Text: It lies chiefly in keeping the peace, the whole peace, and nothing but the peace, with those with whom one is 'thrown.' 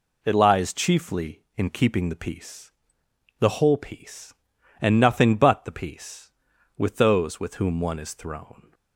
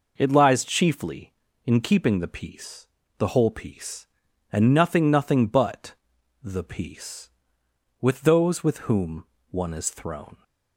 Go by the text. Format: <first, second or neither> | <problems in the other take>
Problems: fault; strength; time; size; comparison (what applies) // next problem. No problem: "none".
first | says "nothing" twice; at 5.0 s // pauses between "but" and "the"; noticeable; at 5.9 s; 0.48 s long // pauses between "whom" and "one"; slight; at 9.2 s; 0.24 s long